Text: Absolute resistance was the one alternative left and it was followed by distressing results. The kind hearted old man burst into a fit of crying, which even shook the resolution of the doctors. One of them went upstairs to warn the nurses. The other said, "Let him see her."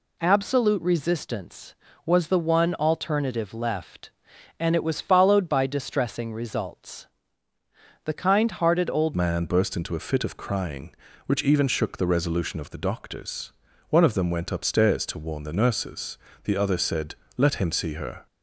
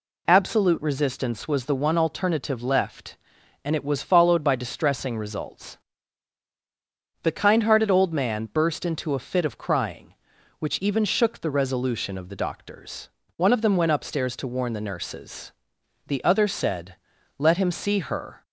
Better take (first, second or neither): second